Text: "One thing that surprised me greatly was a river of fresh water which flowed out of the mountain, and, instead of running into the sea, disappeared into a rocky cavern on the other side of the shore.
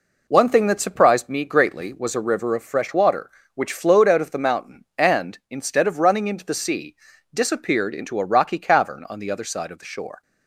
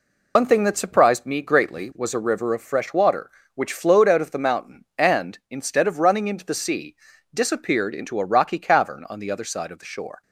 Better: first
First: none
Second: loses the start of "One"; at 0.3 s; 90 ms

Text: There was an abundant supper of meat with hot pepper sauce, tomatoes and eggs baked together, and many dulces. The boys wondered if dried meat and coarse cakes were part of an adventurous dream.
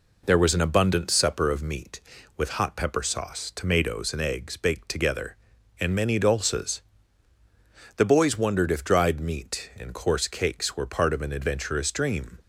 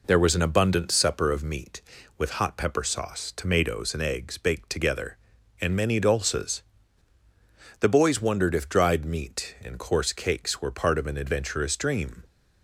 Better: neither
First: none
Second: none

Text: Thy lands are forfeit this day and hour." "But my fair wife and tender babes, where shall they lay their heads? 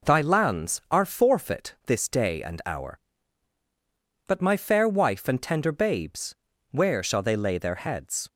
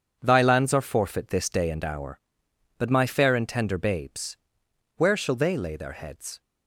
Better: first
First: none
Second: starts louder than the rest; strong; until 1.2 s; 7 dB // skips "wife"; at 3.3 s

